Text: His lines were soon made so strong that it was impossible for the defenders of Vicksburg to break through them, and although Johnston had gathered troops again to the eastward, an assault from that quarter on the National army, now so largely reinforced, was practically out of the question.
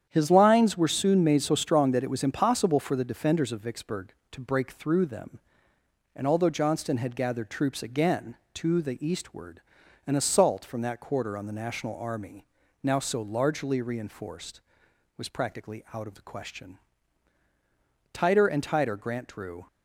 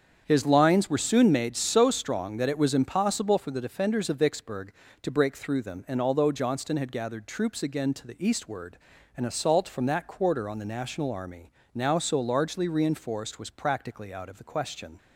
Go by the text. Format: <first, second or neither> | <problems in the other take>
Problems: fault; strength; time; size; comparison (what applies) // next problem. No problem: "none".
second | starts louder than the rest; strong; until 1.0 s; 9 dB; strong in the second // goes on to say "Tighter and tighter Grant drew"; from 18.1 s on; 1.5 s long